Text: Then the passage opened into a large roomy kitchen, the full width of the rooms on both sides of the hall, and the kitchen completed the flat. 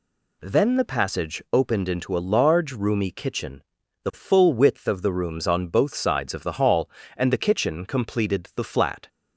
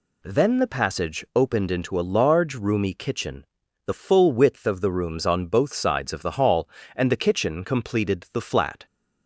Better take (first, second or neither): neither